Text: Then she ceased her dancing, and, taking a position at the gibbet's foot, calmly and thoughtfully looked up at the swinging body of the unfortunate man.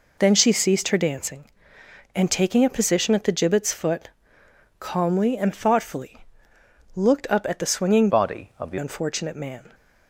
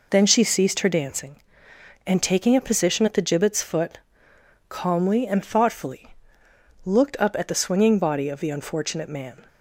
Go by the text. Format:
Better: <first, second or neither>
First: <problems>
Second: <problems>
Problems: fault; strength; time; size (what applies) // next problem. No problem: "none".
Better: second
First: pauses between "thoughtfully" and "looked"; noticeable; at 6.1 s; 0.76 s long // changes voice from "body" to "the"; from 8.0 to 8.7 s; 0.7 s long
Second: pauses between "thoughtfully" and "looked"; noticeable; at 6.0 s; 0.76 s long